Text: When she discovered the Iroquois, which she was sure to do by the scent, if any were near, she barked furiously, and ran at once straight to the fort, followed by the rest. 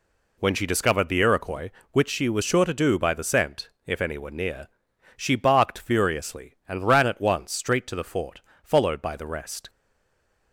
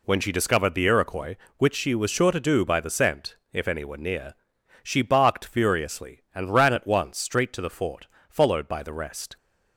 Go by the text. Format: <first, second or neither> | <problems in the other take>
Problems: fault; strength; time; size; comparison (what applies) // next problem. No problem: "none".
second | stays silent after the last word; slight; from 9.6 s on; 0.9 s long